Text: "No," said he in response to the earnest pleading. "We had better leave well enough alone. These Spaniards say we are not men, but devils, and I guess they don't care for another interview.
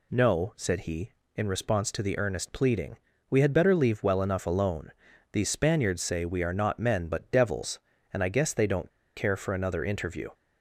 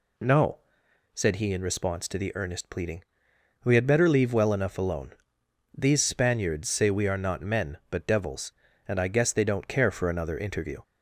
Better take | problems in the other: second | pauses between "don't" and "care"; slight; at 8.8 s; 0.27 s long

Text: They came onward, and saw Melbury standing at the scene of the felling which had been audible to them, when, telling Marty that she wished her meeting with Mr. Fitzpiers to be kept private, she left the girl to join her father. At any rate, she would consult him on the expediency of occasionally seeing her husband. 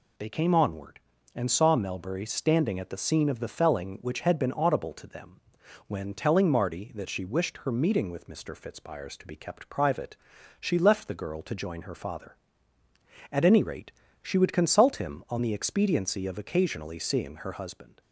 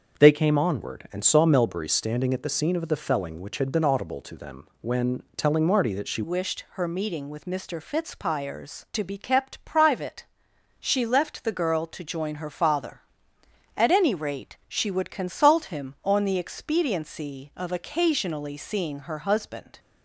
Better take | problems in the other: first | starts louder than the rest; until 1.2 s; 6.5 dB // changes voice at "wished"; from 6.2 s on; 13.5 s long

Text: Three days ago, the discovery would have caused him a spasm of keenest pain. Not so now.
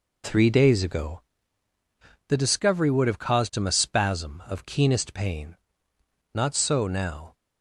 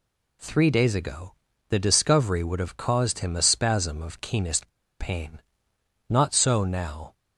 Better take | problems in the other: first | pauses between "keenest" and "pain"; slight; at 4.6 s; 0.30 s long

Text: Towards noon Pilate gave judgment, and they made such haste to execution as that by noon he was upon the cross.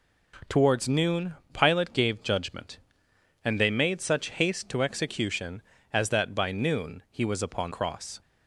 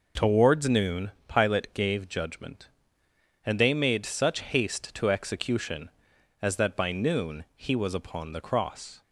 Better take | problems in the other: second | pauses between "noon" and "Pilate"; slight; at 1.3 s; 0.18 s long; slight in the second // skips "the"; at 7.7 s

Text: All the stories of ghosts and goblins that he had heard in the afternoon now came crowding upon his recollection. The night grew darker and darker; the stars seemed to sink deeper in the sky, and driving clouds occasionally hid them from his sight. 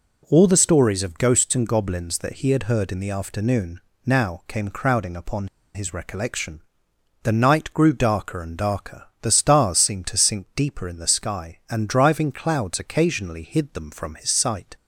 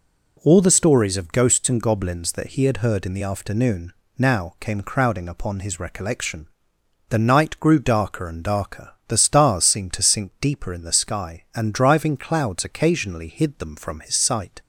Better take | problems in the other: second | pauses between "afternoon" and "now"; slight; at 3.8 s; 0.24 s long; slight in the second // pauses between "upon" and "his"; slight; at 5.4 s; 0.26 s long

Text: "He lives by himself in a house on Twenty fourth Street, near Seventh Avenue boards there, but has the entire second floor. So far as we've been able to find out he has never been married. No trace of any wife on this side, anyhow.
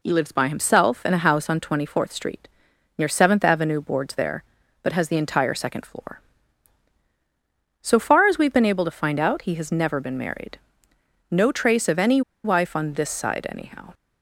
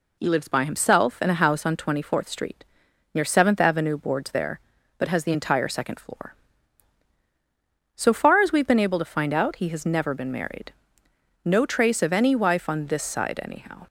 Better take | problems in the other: second | pauses between "any" and "wife"; slight; at 12.2 s; 0.23 s long

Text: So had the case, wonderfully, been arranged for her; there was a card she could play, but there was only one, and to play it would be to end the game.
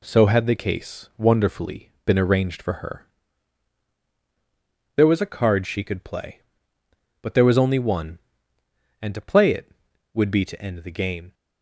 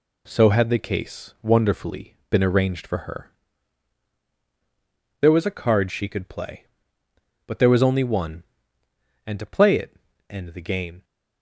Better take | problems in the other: first | skips "would be to"; at 10.1 s

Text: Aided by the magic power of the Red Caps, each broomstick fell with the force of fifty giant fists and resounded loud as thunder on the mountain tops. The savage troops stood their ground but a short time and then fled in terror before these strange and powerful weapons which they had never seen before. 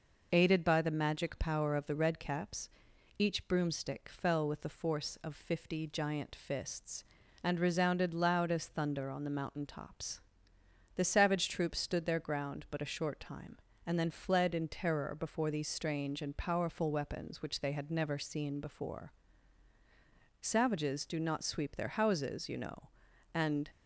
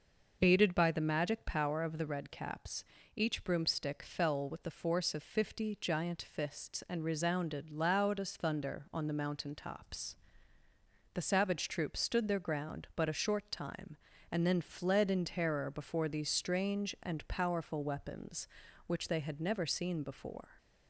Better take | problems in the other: second | goes on to say "Savages do not sweep their houses you know and"; strong; from 20.4 s on; 3.2 s long

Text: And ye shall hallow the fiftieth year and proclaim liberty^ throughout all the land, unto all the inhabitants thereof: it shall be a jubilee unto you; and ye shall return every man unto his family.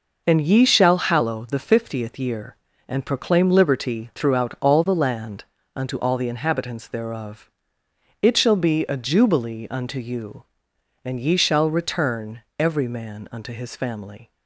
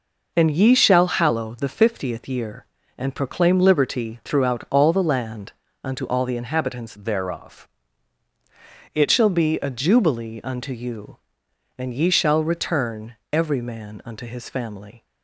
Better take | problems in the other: first | changes voice from "thereof" to "it"; from 6.9 to 9.0 s; 2.1 s long // pauses between "return" and "every"; slight; at 13.1 s; 0.16 s long; slight in the first

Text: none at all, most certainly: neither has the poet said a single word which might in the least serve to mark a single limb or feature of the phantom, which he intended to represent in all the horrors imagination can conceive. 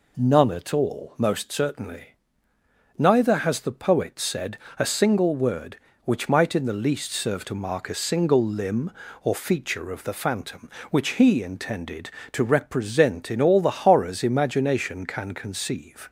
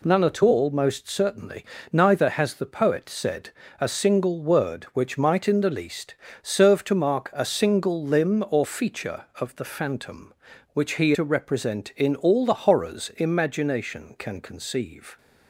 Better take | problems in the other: first | pauses between "said" and "a"; slight; at 3.5 s; 0.28 s long; slight in the first // pauses between "least" and "serve"; slight; at 6.1 s; 0.26 s long // skips "intended"; at 11.1 s

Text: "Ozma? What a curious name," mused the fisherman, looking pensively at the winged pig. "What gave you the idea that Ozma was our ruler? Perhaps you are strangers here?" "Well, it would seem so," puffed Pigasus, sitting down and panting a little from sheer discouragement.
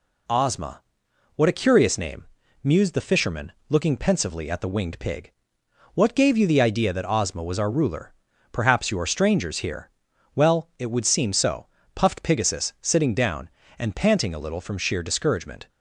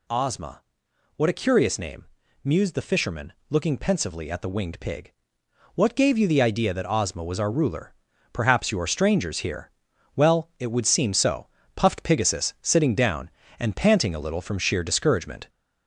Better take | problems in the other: first | gets louder; throughout; 4 dB

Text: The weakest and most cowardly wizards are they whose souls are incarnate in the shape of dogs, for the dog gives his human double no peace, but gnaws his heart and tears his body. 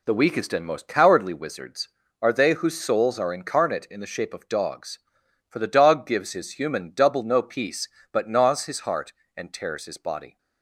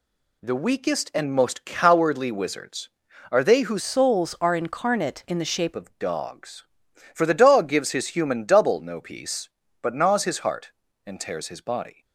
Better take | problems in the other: first | changes voice from "souls" to "shape"; from 3.8 to 5.7 s; 1.9 s long

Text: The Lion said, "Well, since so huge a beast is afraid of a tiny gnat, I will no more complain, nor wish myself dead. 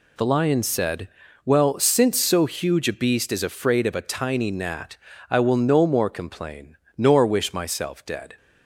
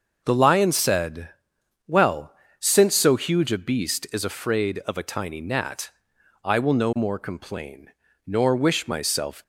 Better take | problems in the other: first | starts louder than the rest; until 1.2 s; 6 dB // stops before "dead"; at 9.4 s

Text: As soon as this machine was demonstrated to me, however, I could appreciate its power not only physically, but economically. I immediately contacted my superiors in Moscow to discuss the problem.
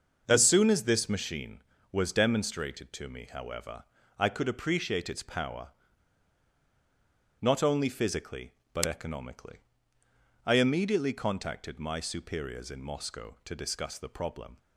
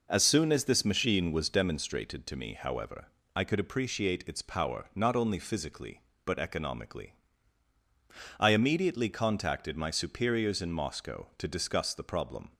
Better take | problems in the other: second | starts louder than the rest; until 1.2 s; 6.5 dB // pauses between "power" and "not"; strong; at 5.6 s; 1.7 s long

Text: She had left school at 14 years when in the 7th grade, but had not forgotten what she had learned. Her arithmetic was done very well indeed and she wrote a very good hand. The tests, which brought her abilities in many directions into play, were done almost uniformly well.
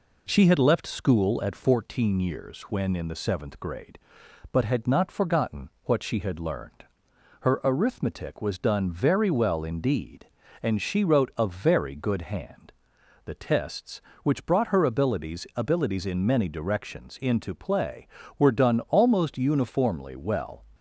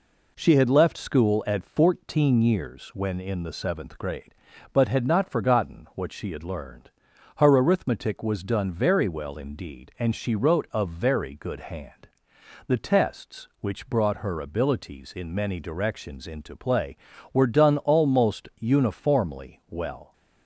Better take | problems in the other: second | pauses between "forgotten" and "what"; slight; at 5.6 s; 0.16 s long // says "abilities" twice; at 15.5 s

